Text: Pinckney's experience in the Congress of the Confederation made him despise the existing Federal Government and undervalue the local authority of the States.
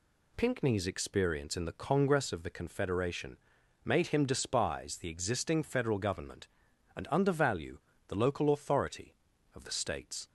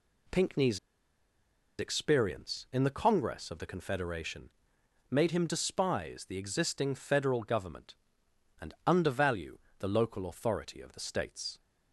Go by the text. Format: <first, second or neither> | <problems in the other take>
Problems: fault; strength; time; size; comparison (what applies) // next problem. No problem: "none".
first | pauses between "Pinckney's" and "experience"; at 0.7 s; 1.0 s long // pauses between "Confederation" and "made"; noticeable; at 4.4 s; 0.60 s long; noticeable in the first // pauses between "undervalue" and "the"; slight; at 9.5 s; 0.22 s long; slight in the first